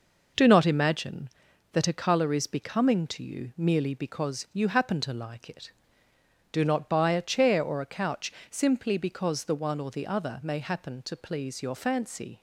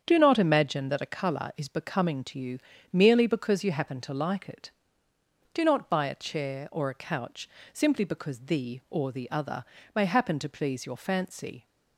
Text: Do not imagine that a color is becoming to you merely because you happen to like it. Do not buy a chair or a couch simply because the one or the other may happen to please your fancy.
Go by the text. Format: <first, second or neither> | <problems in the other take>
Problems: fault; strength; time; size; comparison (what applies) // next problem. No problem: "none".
first | starts louder than the rest; strong; until 1.0 s; 7.5 dB // pauses between "you" and "merely"; slight; at 2.5 s; 0.34 s long // pauses between "couch" and "simply"; slight; at 7.4 s; 0.24 s long; slight in the first // skips "one"; at 8.8 s // pauses between "other" and "may"; slight; at 9.6 s; 0.30 s long